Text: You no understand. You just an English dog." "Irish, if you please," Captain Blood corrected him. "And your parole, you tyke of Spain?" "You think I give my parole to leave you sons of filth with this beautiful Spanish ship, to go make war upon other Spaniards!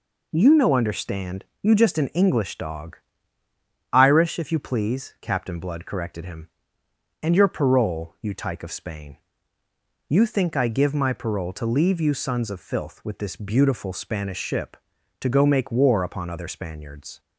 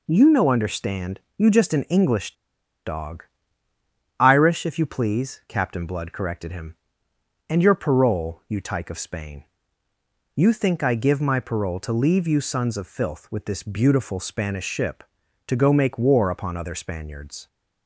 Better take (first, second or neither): first